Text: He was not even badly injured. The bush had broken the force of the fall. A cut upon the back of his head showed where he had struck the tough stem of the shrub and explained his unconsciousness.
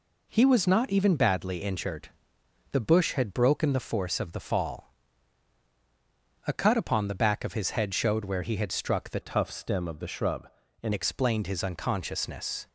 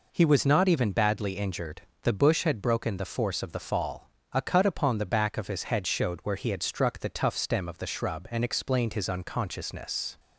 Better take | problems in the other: second | changes voice from "tough" to "and"; from 9.2 to 10.9 s; 1.7 s long

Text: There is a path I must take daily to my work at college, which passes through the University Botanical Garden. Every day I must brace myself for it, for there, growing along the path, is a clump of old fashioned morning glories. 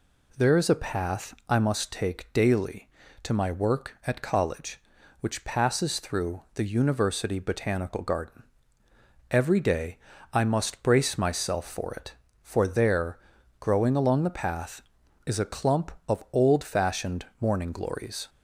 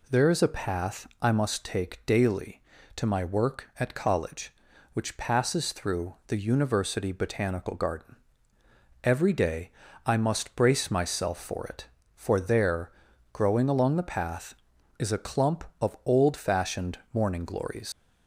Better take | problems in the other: first | pauses between "day" and "I"; slight; at 9.6 s; 0.36 s long; slight in the first // pauses between "fashioned" and "morning"; slight; at 16.9 s; 0.16 s long; slight in the first // leaves "glories" unfinished; at 17.9 s; 95 ms

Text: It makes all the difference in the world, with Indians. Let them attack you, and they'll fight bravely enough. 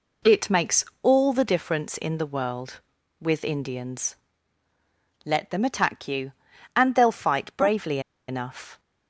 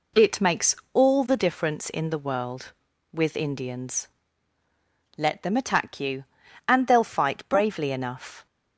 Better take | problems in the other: second | pauses between "makes" and "all"; slight; at 0.8 s; 0.16 s long; slight in the second // pauses between "bravely" and "enough"; slight; at 7.9 s; 0.28 s long

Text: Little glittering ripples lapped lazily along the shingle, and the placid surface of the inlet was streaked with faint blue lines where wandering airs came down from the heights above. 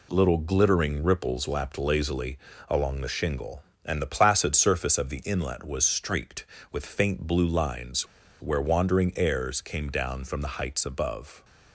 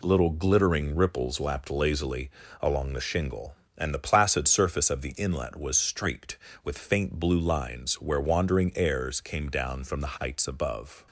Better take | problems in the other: second | pauses between "lazily" and "along"; slight; at 2.3 s; 0.30 s long; slight in the second // pauses between "lines" and "where"; slight; at 8.0 s; 0.35 s long

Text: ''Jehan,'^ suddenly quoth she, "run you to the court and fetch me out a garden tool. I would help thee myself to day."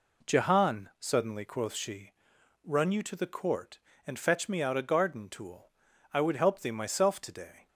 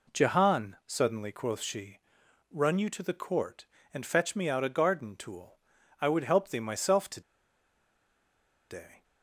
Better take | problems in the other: first | pauses between "to" and "day"; strong; at 7.2 s; 1.4 s long

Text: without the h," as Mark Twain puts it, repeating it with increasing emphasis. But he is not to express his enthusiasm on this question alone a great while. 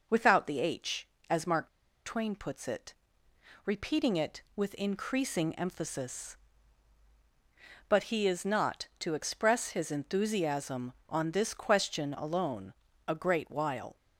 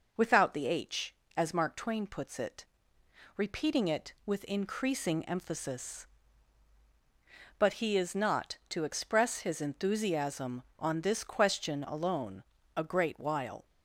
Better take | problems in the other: second | pauses between "Mark" and "Twain"; at 1.6 s; 0.37 s long // pauses between "alone" and "a"; slight; at 12.7 s; 0.34 s long; slight in the second

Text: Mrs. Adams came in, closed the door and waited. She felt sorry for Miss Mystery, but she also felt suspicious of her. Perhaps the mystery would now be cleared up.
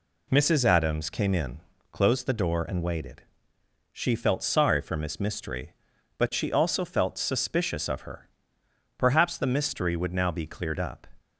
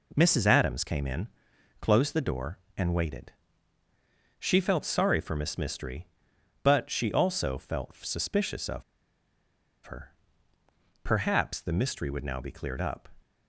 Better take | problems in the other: first | pauses between "of" and "her"; at 8.8 s; 1.0 s long

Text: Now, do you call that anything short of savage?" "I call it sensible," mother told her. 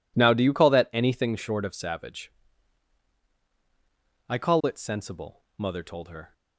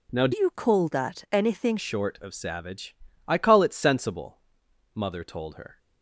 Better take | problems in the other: first | changes voice from "you" to "anything"; from 0.3 to 1.7 s; 1.4 s long

